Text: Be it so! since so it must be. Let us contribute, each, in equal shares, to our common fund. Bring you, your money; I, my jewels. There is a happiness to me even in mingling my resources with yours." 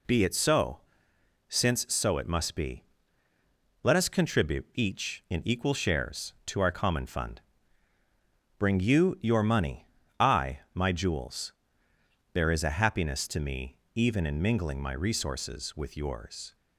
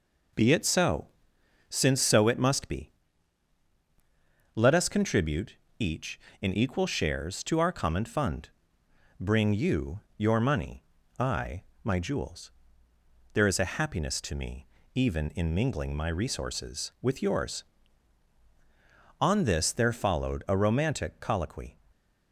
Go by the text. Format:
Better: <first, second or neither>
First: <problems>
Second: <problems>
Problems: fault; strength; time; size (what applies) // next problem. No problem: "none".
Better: first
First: pauses between "me" and "even"; slight; at 13.7 s; 0.20 s long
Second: pauses between "me" and "even"; slight; at 14.6 s; 0.30 s long // goes on to say "On this there followed a romantic colloquy"; strong; from 19.1 s on; 2.5 s long